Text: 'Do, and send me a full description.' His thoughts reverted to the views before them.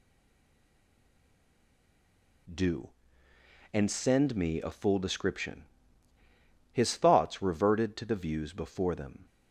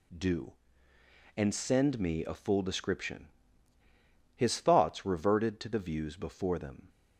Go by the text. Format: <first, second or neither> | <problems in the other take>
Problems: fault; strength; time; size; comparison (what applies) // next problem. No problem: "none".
second | stays silent before the first word; until 2.4 s; 2.4 s long